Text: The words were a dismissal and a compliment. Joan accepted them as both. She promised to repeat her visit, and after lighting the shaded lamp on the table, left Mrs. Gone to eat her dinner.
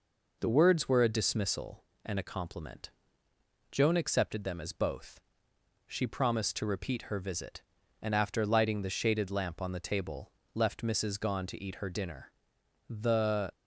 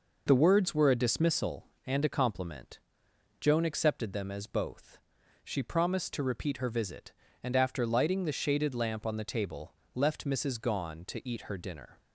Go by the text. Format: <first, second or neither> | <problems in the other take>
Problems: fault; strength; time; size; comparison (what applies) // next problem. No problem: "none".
second | goes on to say "The"; noticeable; from 12.8 s on; 0.62 s long